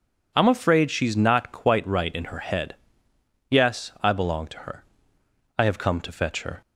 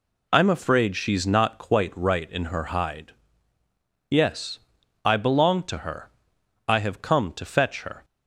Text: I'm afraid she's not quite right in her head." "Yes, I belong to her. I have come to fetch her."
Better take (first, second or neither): first